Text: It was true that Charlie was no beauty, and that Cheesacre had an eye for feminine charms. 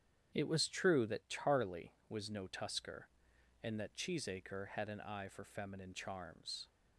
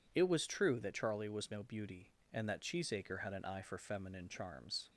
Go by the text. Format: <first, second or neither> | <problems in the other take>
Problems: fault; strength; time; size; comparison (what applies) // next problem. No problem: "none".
second | starts louder than the rest; strong; until 1.3 s; 8.5 dB // says "tusker" for "beauty"; at 2.4 s